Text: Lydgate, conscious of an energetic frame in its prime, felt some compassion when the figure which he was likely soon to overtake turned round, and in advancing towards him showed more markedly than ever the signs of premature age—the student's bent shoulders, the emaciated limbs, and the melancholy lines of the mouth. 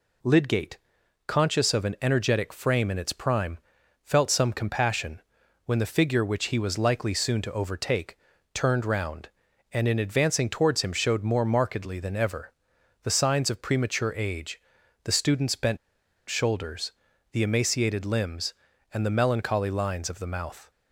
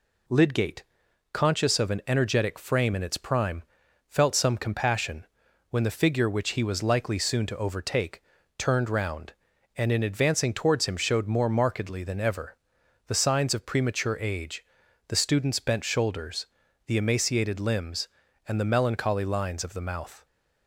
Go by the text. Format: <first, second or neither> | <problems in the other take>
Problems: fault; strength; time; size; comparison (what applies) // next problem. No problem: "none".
second | pauses between "compassion" and "when"; at 5.2 s; 0.42 s long; also in the second // pauses between "overtake" and "turned"; slight; at 8.1 s; 0.34 s long; slight in the second // pauses between "ever" and "the"; noticeable; at 12.5 s; 0.50 s long; noticeable in the second // pauses between "bent" and "shoulders"; noticeable; at 15.7 s; 0.52 s long